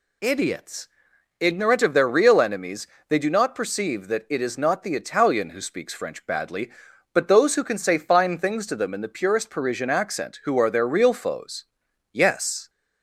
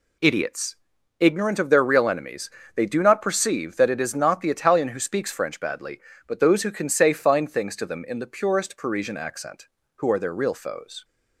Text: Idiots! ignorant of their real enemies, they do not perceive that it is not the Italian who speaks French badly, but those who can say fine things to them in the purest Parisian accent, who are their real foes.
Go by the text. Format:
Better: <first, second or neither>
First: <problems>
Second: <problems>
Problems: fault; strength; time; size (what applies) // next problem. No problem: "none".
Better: second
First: goes on to say "Yes"; from 12.1 s on; 0.58 s long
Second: none